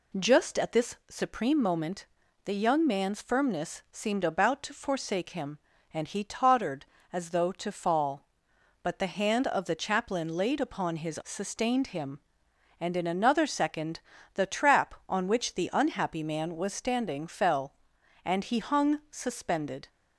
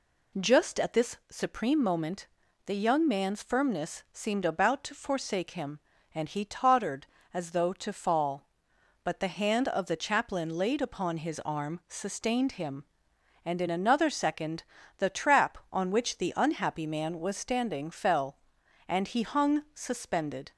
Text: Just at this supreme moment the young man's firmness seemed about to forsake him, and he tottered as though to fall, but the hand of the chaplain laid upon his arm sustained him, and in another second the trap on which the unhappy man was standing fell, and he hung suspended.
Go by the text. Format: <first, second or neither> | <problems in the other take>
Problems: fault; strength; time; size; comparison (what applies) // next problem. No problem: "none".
second | pauses between "moment" and "the"; at 2.0 s; 0.40 s long; also in the second // skips "arm"; at 11.2 s // pauses between "second" and "the"; slight; at 13.9 s; 0.34 s long; slight in the second